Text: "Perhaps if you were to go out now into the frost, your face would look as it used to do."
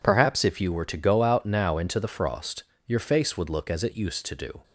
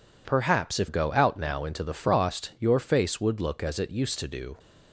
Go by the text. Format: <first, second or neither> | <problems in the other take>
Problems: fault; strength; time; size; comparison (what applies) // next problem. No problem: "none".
first | skips "you were to"; at 0.8 s